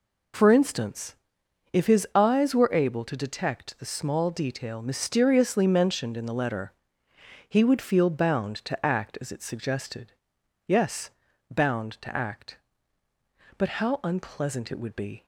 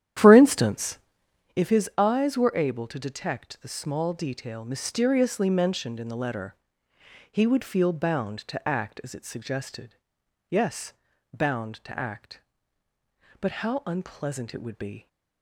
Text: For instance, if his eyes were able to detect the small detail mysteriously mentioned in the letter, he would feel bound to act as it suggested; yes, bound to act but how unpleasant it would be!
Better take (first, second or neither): first